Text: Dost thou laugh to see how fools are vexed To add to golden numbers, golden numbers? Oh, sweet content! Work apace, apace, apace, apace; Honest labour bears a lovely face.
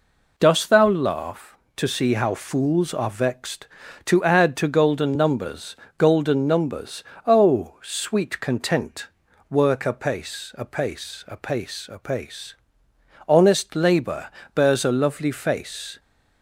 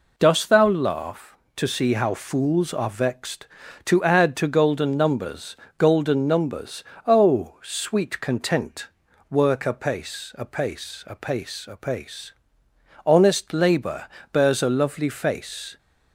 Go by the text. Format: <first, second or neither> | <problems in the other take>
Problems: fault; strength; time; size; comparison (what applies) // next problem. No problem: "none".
neither | pauses between "labour" and "bears"; slight; the same in both